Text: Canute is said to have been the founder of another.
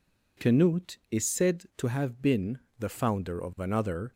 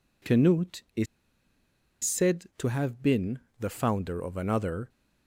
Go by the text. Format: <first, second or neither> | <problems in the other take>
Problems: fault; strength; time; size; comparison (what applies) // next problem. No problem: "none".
first | pauses between "is" and "said"; at 1.0 s; 0.98 s long // pauses between "been" and "the"; slight; at 3.4 s; 0.18 s long; slight in the first